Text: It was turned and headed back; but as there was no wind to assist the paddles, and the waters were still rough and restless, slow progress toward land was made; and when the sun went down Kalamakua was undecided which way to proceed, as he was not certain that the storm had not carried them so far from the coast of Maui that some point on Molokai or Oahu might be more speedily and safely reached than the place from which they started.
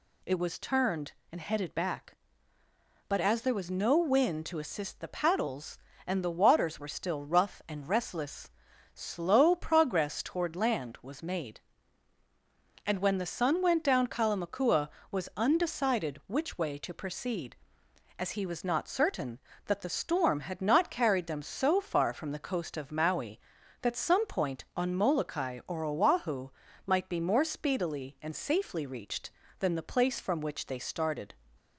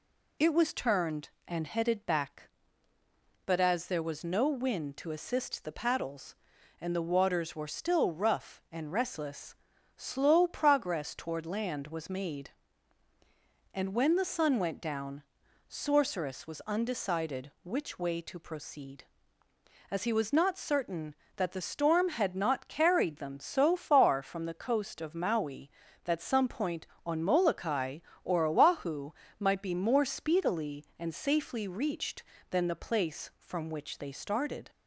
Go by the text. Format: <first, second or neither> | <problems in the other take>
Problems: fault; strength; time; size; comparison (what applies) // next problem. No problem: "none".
first | says "Sorceress" for "Kalamakua"; at 15.6 s // pauses between "Oahu" and "might"; slight; at 29.1 s; 0.28 s long; slight in the first